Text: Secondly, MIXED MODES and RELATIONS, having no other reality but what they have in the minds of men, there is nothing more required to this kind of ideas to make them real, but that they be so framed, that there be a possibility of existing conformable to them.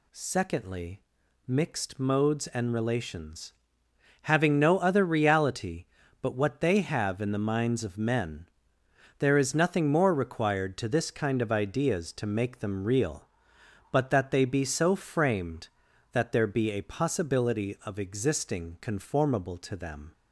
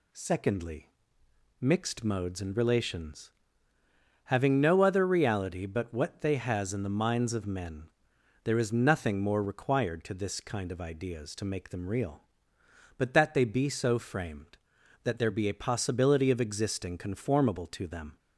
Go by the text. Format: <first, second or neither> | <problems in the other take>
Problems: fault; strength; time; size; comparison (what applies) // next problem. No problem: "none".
first | says "has" for "have"; at 6.3 s